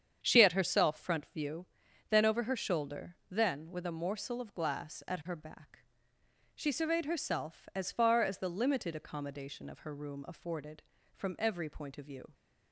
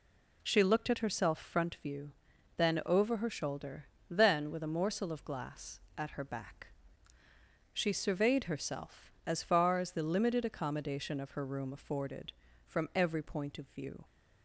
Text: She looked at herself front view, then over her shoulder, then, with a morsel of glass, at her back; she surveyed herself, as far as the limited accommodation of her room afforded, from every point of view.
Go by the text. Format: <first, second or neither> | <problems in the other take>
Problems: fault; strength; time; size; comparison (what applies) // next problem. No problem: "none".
second | starts louder than the rest; strong; until 1.2 s; 8 dB // skips "looked"; at 0.4 s